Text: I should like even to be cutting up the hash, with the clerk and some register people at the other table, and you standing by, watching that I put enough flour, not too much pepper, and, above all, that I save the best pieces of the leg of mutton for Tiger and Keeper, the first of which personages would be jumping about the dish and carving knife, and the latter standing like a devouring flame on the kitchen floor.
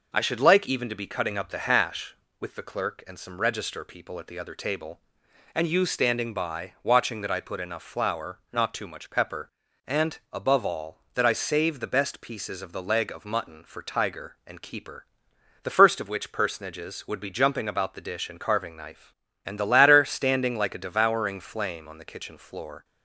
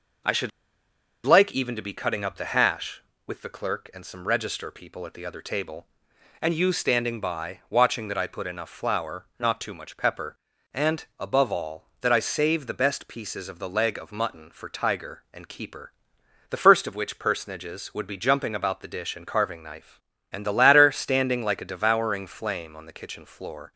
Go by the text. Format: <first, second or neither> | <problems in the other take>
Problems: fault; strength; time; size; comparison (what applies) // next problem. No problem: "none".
first | pauses between "should" and "like"; noticeable; at 0.5 s; 0.75 s long